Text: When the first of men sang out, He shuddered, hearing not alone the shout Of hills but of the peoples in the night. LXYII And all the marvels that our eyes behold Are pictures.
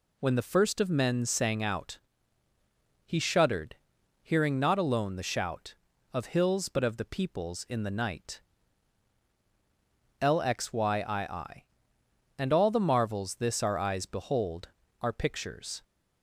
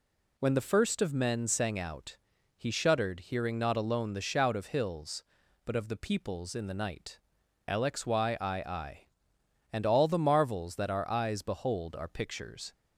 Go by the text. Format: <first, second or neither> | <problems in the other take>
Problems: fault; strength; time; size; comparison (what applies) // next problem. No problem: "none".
second | says "this" for "that"; at 13.3 s